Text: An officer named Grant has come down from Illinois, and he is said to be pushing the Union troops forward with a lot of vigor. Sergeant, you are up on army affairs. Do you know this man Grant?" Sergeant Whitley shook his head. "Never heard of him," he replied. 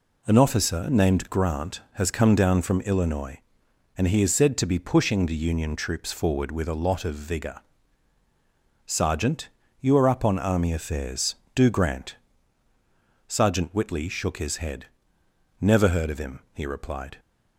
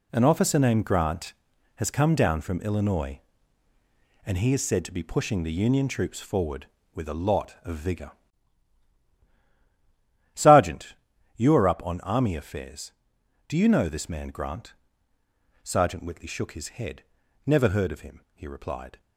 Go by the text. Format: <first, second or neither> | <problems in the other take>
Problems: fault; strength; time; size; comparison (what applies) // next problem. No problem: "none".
second | skips "you know this man"; at 11.6 s